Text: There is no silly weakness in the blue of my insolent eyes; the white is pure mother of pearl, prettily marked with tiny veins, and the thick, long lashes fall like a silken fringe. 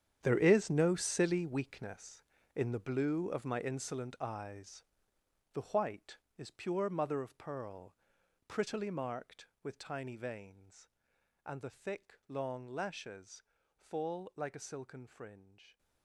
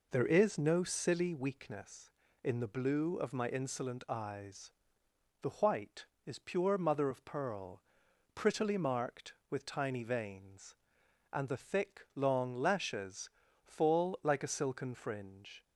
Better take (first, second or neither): second